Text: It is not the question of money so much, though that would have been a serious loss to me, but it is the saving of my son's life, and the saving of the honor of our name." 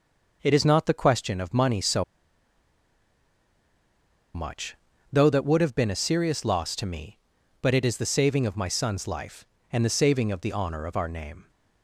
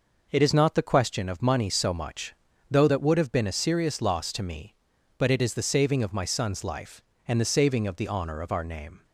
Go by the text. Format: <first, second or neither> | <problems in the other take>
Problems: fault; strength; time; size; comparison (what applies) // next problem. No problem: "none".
second | pauses between "so" and "much"; strong; at 2.0 s; 2.3 s long